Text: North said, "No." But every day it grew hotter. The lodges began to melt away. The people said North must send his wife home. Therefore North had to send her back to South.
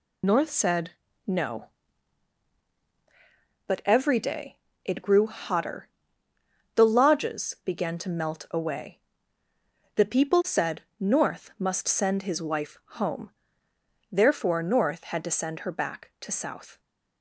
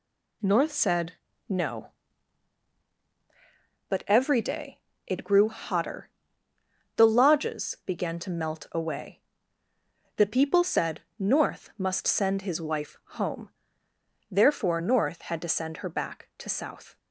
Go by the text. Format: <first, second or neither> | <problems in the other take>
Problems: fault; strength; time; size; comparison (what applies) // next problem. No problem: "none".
second | loses the start of "North"; at 0.2 s; 40 ms // pauses between "day" and "it"; slight; at 4.5 s; 0.26 s long; slight in the second // pauses between "said" and "North"; slight; at 10.8 s; 0.18 s long; slight in the second // pauses between "wife" and "home"; slight; at 12.7 s; 0.22 s long; slight in the second